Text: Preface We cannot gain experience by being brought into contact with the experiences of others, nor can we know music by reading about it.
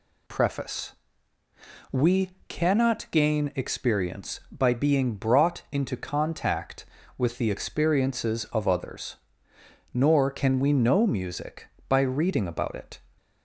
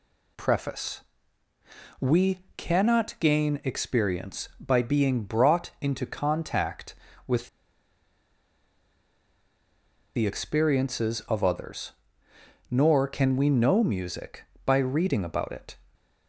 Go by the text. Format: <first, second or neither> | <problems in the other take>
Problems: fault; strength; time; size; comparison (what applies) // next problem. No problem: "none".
first | pauses between "Preface" and "We"; at 1.0 s; 1.0 s long; also in the first // pauses between "We" and "cannot"; slight; at 2.4 s; 0.16 s long; slight in the first // pauses between "with" and "the"; strong; at 7.4 s; 2.6 s long